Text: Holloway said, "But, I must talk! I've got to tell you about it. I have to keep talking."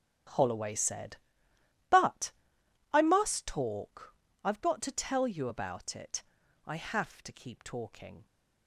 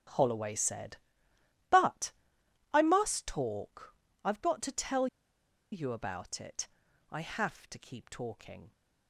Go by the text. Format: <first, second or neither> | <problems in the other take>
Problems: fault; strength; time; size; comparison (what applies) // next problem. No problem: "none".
first | starts louder than the rest; strong; until 1.8 s; 10 dB; strong in the first // pauses between "tell" and "you"; noticeable; at 5.0 s; 0.66 s long